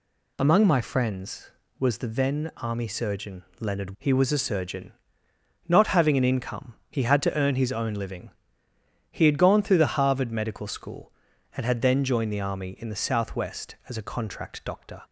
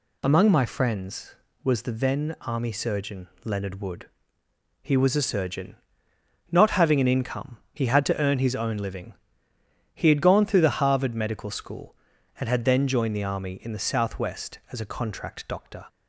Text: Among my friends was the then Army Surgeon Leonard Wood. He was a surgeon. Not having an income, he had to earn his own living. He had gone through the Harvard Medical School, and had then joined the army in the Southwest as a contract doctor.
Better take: second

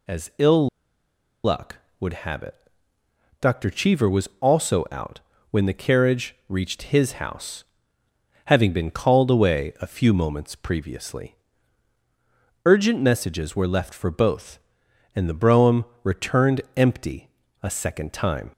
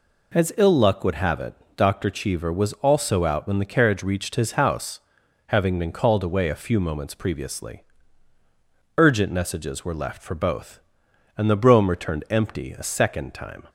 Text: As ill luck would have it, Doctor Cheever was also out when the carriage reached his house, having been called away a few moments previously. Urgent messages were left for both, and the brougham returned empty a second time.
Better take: second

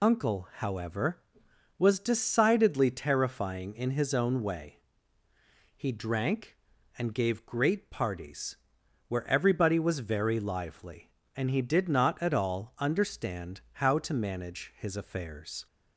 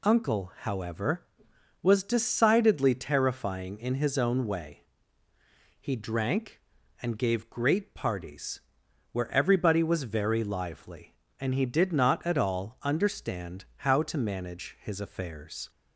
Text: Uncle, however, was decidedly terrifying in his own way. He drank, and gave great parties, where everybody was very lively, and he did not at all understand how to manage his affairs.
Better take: second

